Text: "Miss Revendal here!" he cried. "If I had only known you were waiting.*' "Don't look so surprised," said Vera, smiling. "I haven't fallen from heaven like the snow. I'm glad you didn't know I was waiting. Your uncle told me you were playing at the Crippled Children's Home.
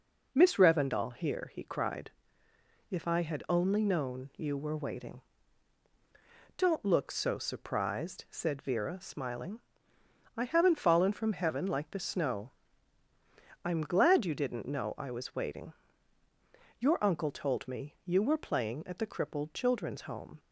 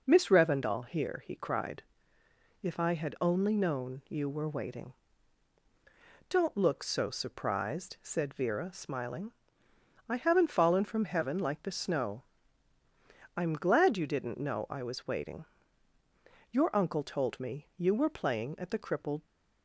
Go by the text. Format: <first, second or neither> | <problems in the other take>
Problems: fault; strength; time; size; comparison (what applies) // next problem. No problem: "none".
first | stops before "Children's Home"; at 19.2 s